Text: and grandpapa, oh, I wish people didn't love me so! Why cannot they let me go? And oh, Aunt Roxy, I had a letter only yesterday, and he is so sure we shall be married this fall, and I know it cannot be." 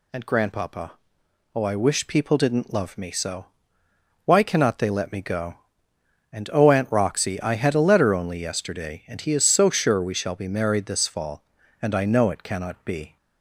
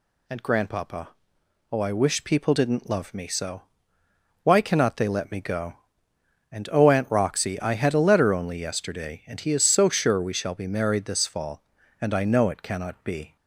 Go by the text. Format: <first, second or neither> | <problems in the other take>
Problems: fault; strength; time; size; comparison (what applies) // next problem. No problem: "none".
neither | none